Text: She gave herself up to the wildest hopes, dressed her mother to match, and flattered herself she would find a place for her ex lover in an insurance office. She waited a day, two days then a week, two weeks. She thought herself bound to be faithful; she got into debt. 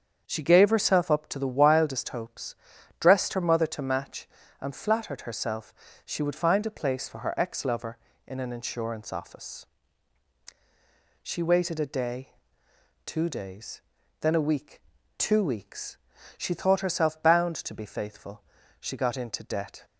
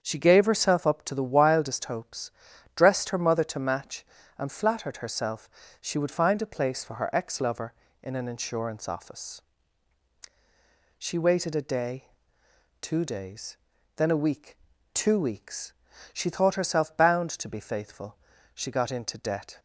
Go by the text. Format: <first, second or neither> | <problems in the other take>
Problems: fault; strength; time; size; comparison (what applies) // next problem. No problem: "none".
neither | starts louder than the rest; strong; the same in both // pauses between "herself" and "she"; slight; the same in both // pauses between "days" and "then"; the same in both